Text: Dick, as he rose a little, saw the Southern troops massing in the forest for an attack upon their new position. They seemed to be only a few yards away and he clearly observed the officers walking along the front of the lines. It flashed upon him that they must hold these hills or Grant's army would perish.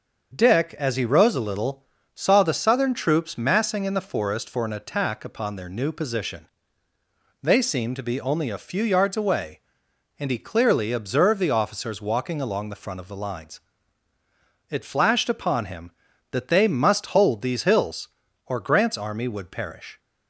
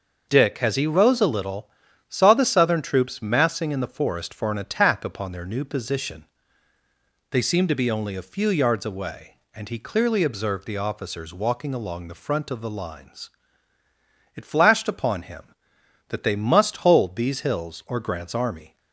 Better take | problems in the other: first | starts louder than the rest; until 1.2 s; 6.5 dB; also in the first // stops before "would perish"; at 18.7 s

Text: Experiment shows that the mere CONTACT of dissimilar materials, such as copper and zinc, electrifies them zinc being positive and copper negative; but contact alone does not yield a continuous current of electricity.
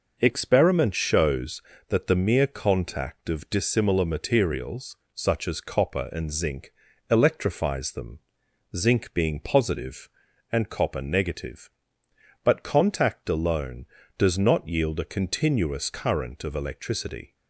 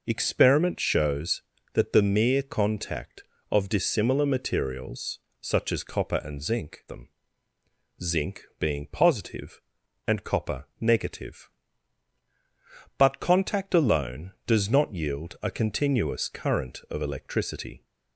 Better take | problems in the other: first | skips "electrifies"; at 6.8 s // pauses between "them" and "zinc"; noticeable; at 7.0 s; 0.92 s long; noticeable in the first // pauses between "zinc" and "being"; slight; at 8.4 s; 0.16 s long // pauses between "copper" and "negative"; slight; at 10.6 s; 0.16 s long

